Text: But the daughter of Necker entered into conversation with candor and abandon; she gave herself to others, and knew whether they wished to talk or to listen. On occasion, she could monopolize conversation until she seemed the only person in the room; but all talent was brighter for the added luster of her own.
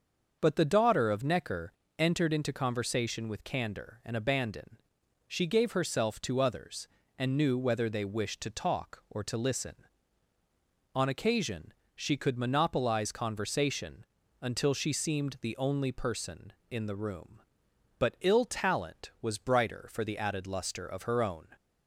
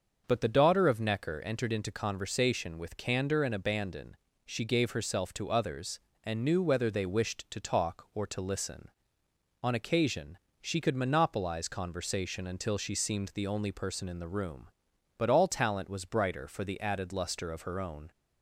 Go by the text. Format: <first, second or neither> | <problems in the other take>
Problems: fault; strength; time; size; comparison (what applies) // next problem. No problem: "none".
second | starts louder than the rest; until 1.4 s; 6.5 dB; also in the second // pauses between "Necker" and "entered"; slight; at 1.7 s; 0.26 s long // pauses between "conversation" and "until"; at 14.0 s; 0.38 s long // says "ill" for "all"; at 18.2 s